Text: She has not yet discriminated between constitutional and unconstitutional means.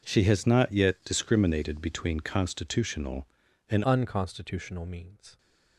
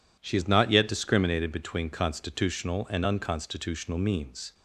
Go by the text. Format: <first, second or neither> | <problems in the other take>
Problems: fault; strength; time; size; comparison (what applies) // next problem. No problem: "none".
second | changes voice at "unconstitutional"; from 3.8 s on; 1.5 s long